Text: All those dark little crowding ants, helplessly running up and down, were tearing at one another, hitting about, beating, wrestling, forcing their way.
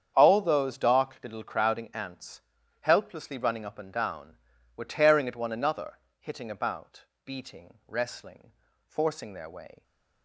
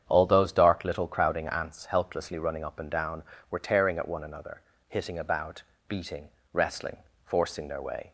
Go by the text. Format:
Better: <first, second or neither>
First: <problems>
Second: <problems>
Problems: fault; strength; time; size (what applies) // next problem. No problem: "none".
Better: neither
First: starts louder than the rest; strong; until 1.1 s; 8.5 dB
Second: starts louder than the rest; strong; until 1.0 s; 8.5 dB